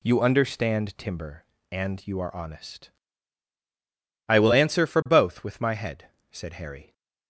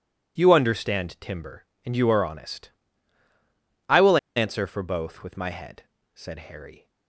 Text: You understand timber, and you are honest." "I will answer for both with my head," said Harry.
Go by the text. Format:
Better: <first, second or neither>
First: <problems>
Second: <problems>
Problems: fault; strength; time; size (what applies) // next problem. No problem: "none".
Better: first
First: none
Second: pauses between "will" and "answer"; slight; at 4.1 s; 0.18 s long